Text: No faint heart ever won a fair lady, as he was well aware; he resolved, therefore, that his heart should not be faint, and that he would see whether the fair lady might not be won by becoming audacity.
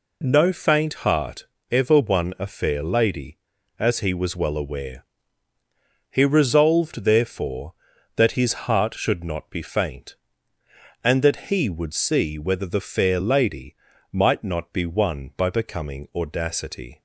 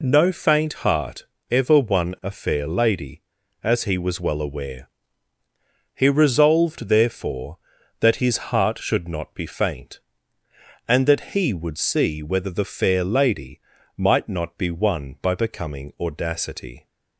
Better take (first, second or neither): neither